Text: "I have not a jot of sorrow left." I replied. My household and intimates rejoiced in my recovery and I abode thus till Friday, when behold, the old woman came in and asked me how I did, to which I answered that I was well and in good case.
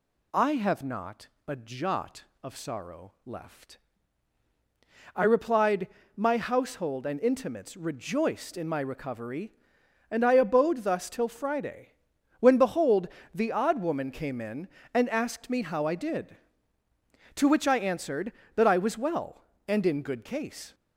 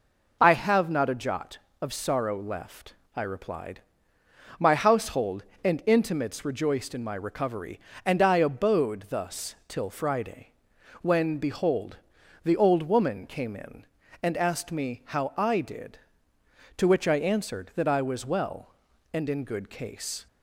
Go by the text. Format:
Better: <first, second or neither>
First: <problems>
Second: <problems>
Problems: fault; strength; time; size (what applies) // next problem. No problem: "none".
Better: second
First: pauses between "not" and "a"; slight; at 1.2 s; 0.18 s long // says "odd" for "old"; at 13.5 s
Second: none